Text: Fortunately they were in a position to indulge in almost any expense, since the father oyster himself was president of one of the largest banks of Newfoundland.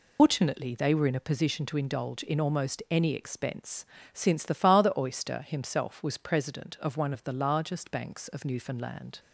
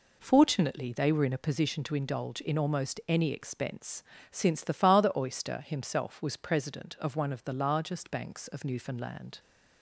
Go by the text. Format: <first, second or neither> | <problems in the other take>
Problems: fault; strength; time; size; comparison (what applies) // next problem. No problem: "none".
second | loses the start of "Fortunately"; at 0.1 s; 175 ms